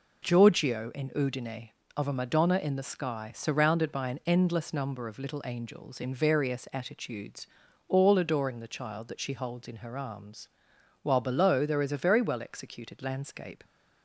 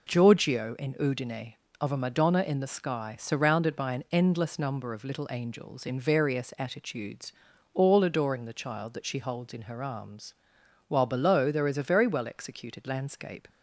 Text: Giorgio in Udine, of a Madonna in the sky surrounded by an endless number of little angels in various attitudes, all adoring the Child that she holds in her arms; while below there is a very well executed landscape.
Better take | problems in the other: neither | none

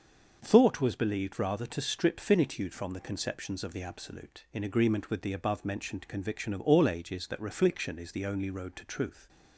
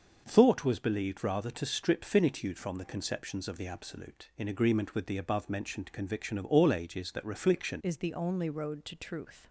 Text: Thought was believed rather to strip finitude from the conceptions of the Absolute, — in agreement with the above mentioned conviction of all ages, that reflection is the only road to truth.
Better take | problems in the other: first | starts louder than the rest; noticeable; until 1.2 s; 6 dB; also in the first // changes voice at "is"; from 7.8 s on; 1.6 s long

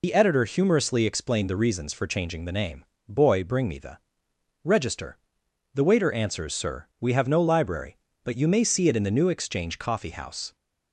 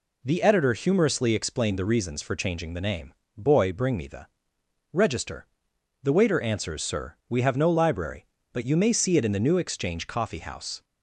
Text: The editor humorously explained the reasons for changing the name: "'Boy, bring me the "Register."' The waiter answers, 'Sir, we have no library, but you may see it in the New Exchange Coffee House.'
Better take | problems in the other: second | loses the start of "The"; at 0.0 s; 85 ms // pauses between "the" and "Register"; noticeable; at 3.9 s; 0.64 s long; noticeable in the second

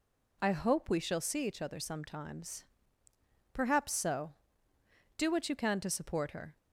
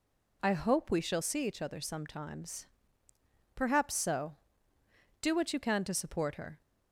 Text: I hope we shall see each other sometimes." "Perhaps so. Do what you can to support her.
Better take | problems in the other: neither | none

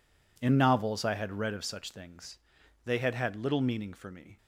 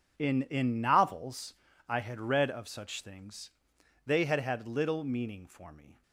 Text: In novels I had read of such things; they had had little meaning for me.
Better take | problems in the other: first | says "In" twice; at 0.4 s // pauses between "novels" and "I"; slight; at 1.5 s; 0.34 s long

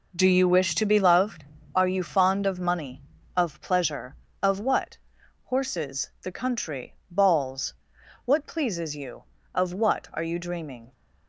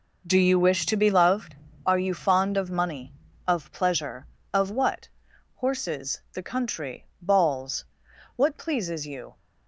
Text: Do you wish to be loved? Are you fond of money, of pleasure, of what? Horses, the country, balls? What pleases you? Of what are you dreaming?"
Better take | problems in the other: first | stops before "Of what are you dreaming"; at 9.3 s

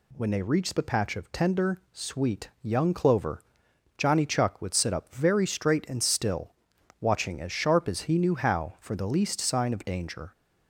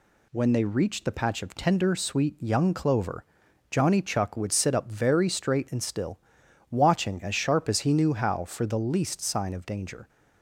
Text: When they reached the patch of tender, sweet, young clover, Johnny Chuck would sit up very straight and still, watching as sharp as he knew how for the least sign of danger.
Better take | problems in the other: neither | none

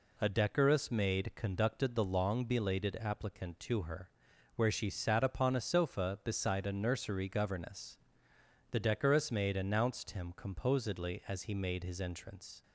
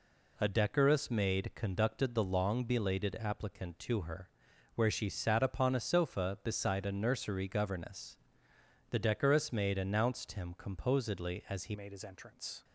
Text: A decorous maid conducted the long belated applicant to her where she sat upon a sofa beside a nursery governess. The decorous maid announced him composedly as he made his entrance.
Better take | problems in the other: first | pauses between "her" and "where"; noticeable; at 4.2 s; 0.46 s long; noticeable in the first // changes voice at "made"; from 11.7 s on; 0.9 s long

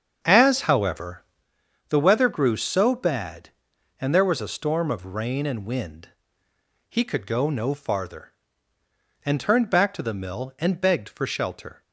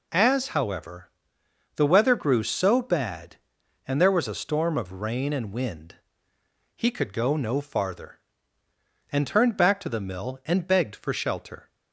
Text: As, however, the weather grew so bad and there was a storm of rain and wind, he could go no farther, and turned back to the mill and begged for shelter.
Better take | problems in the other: second | starts louder than the rest; until 1.5 s; 7 dB

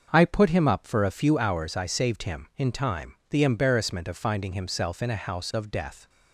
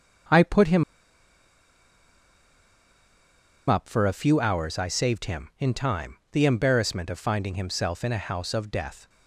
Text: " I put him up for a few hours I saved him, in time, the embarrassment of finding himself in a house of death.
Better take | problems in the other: first | starts louder than the rest; noticeable; until 4.1 s; 6 dB; also in the first // pauses between "him" and "up"; strong; at 0.8 s; 2.8 s long

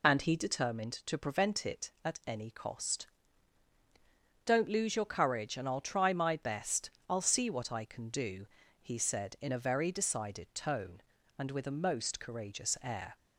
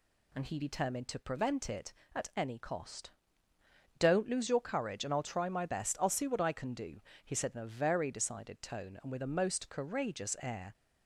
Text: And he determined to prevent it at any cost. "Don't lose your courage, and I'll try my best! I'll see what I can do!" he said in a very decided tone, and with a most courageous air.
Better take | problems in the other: second | loses the start of "And"; at 0.0 s; 25 ms

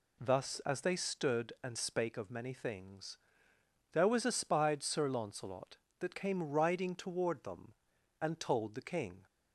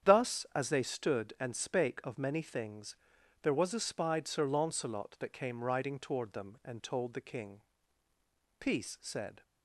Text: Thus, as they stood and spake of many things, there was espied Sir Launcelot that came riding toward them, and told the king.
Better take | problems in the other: first | starts louder than the rest; strong; until 1.1 s; 8.5 dB // goes on to say "Peace said"; noticeable; from 8.6 s on; 0.81 s long

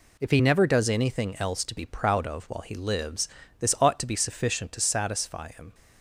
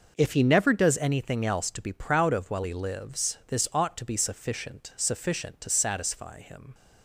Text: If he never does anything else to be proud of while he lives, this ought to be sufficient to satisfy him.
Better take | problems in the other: first | says "sufficient" twice; at 4.9 s

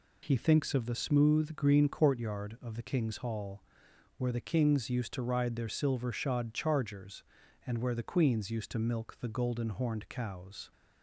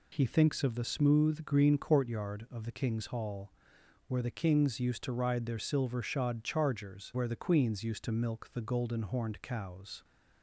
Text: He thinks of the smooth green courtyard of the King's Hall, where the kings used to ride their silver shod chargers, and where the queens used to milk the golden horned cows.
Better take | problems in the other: first | skips "and"; at 7.1 s

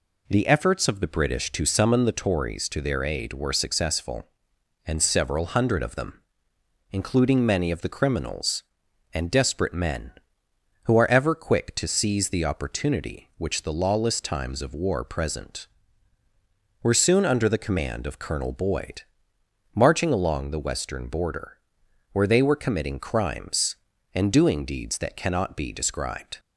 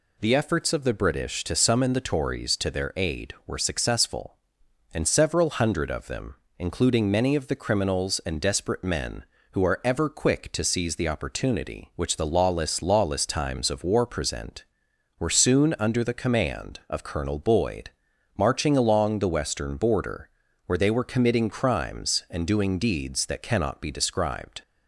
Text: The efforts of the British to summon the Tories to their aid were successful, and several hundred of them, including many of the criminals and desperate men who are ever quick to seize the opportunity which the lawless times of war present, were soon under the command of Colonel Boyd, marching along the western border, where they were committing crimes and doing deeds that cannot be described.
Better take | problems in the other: first | says "lawless" twice; at 12.8 s

